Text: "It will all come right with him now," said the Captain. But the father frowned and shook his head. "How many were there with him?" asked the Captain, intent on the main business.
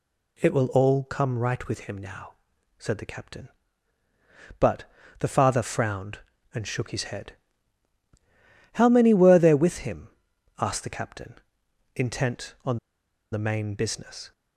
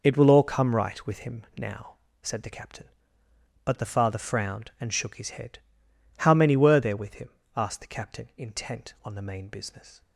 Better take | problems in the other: second | pauses between "But" and "the"; slight; at 4.8 s; 0.36 s long // pauses between "on" and "the"; noticeable; at 12.7 s; 0.55 s long

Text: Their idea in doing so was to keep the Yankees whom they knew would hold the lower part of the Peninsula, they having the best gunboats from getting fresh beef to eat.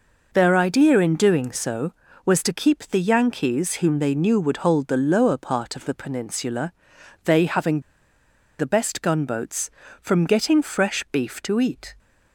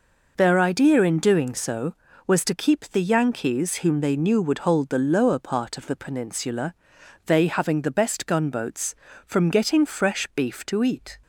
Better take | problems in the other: second | pauses between "having" and "the"; noticeable; at 7.8 s; 0.78 s long

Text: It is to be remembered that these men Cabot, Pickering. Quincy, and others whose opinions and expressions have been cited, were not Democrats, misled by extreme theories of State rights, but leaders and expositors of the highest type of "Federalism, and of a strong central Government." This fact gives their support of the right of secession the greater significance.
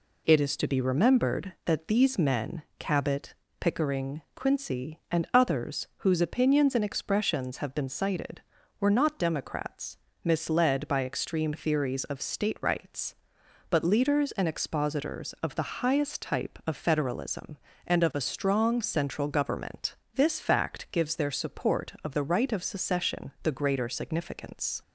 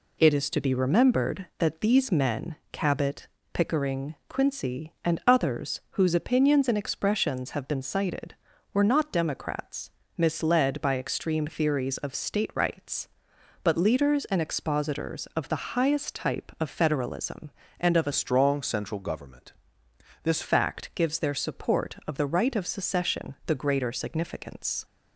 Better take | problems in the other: first | pauses between "men" and "Cabot"; slight; at 2.5 s; 0.16 s long; slight in the first // changes voice from "strong" to "This"; from 18.1 to 20.4 s; 2.3 s long

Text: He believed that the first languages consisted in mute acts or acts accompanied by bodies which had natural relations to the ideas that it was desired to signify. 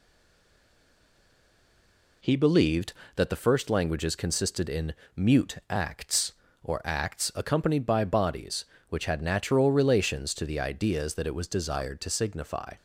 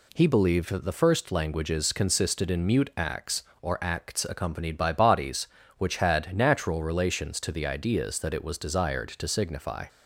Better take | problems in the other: second | stays silent before the first word; until 2.2 s; 2.2 s long // pauses between "in" and "mute"; slight; at 4.9 s; 0.22 s long

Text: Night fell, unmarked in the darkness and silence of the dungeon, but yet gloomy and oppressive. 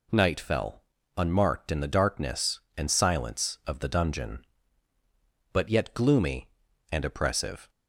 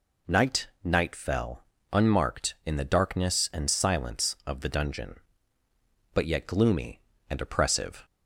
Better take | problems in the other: first | says "Night" twice; at 0.8 s

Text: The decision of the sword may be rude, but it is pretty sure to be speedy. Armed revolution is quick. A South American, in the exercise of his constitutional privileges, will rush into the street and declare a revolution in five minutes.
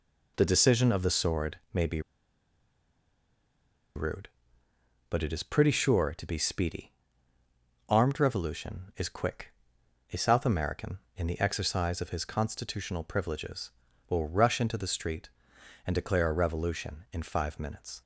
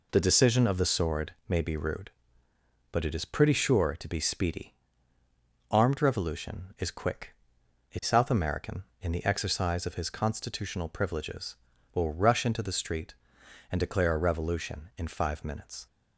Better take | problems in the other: second | pauses between "be" and "rude"; strong; at 2.0 s; 1.9 s long

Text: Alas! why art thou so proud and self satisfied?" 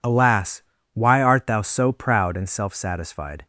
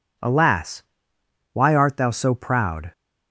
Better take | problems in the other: first | stops before "and self satisfied"; at 2.9 s

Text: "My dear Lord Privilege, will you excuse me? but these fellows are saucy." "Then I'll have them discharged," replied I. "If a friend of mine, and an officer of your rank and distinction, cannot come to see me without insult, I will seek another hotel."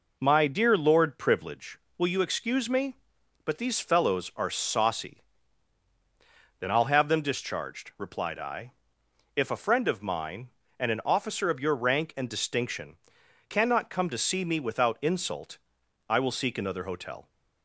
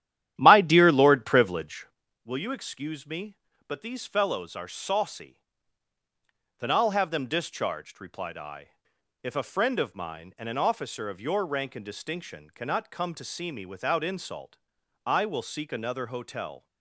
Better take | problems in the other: first | starts louder than the rest; strong; until 1.9 s; 11.5 dB

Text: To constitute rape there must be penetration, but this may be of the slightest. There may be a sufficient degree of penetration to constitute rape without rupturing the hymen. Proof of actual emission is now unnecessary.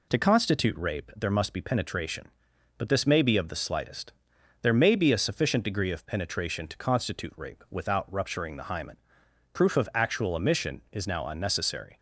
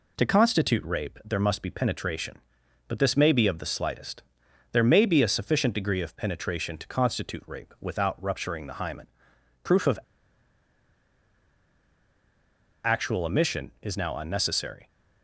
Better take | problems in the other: first | pauses between "of" and "actual"; strong; at 9.9 s; 2.8 s long

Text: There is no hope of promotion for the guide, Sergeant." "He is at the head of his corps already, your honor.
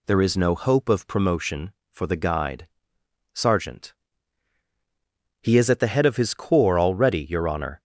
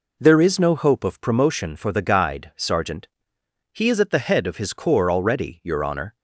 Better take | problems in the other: neither | none

